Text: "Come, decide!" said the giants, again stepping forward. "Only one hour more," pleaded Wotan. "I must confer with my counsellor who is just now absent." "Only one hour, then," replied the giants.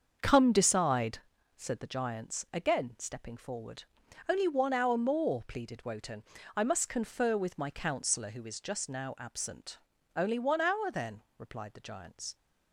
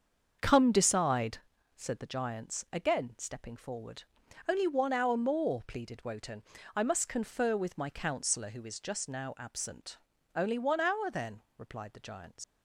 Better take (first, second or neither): first